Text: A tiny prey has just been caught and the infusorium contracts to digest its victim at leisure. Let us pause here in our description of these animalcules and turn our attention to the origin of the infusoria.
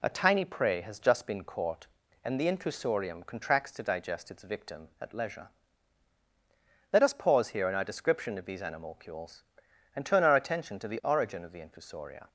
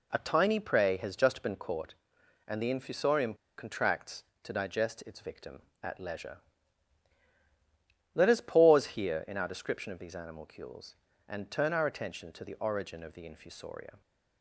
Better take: first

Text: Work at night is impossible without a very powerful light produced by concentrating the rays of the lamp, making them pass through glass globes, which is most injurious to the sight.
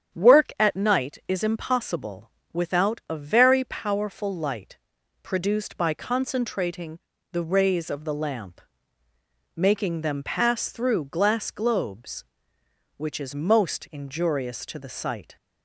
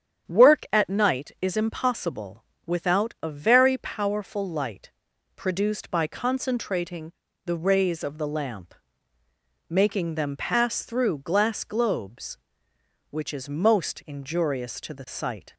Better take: neither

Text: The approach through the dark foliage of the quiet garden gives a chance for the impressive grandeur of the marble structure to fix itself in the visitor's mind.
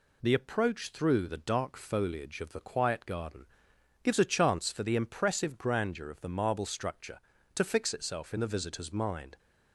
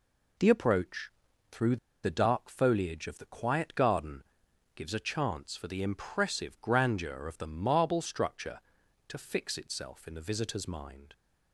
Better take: first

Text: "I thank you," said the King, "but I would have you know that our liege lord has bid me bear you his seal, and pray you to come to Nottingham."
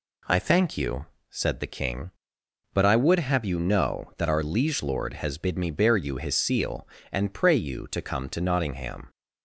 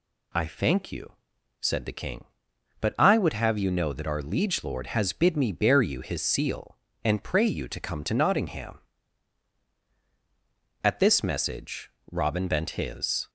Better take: first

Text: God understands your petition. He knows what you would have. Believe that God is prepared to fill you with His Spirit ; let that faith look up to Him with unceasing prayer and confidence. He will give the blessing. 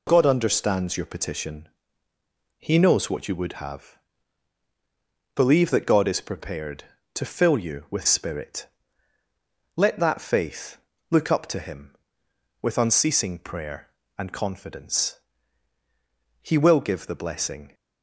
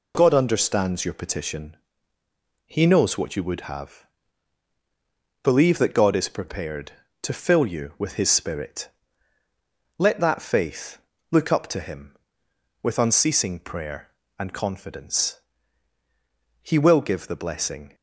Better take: second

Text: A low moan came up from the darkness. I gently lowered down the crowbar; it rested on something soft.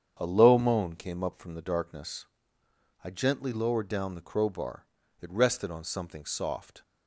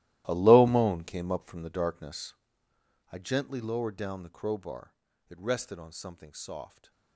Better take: first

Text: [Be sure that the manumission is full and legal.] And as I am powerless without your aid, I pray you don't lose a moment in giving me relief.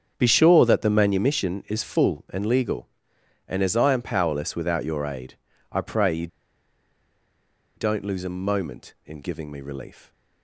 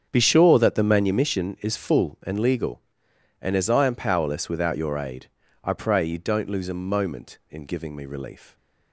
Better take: second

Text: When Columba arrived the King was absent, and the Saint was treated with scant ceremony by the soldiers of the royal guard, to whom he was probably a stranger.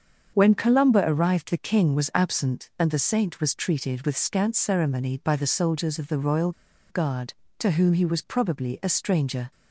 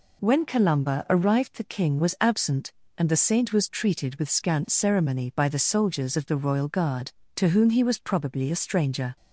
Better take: second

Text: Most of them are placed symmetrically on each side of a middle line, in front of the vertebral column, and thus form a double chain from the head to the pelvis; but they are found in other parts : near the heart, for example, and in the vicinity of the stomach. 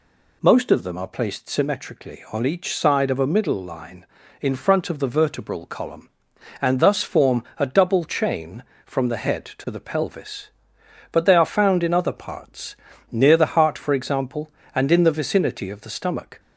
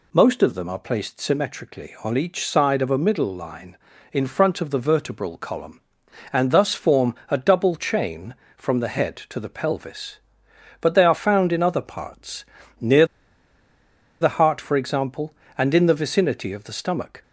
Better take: first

